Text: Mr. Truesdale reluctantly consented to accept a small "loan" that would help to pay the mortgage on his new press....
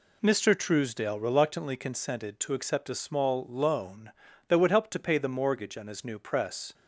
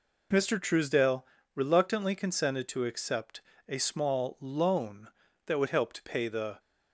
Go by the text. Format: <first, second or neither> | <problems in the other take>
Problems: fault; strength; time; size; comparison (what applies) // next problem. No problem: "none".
first | pauses between "Truesdale" and "reluctantly"; slight; at 1.2 s; 0.30 s long // pauses between "accept" and "a"; slight; at 3.4 s; 0.26 s long // stops before "mortgage on his new press"; at 6.5 s